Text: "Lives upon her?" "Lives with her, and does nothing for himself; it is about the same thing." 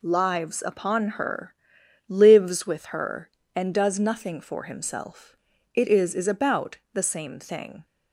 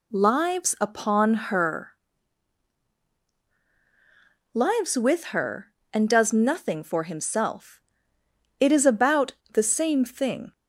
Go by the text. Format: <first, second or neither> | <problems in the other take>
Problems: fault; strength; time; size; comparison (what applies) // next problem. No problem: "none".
second | says "is" twice; at 6.1 s // pauses between "about" and "the"; slight; at 6.7 s; 0.16 s long; slight in the second